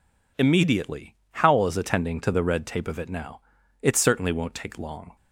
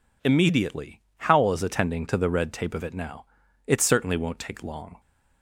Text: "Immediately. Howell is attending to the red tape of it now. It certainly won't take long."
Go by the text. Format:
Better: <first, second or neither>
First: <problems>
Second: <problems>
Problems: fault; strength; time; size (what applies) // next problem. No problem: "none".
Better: neither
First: none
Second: none